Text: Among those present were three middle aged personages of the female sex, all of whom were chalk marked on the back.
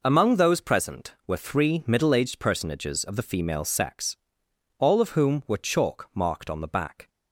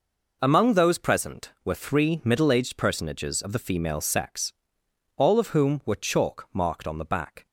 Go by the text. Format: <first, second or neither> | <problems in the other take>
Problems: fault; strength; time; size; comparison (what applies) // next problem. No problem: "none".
neither | none